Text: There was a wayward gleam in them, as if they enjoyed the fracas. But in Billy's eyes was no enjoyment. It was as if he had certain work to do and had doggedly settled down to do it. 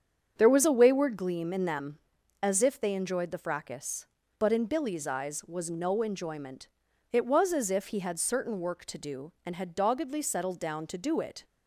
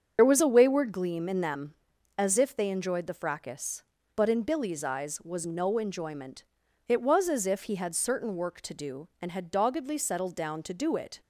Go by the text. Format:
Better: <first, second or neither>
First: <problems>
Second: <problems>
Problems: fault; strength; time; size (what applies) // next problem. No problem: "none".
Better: first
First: starts louder than the rest; strong; until 1.3 s; 7.5 dB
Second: loses the start of "There"; at 0.1 s; 55 ms // starts louder than the rest; until 1.1 s; 7 dB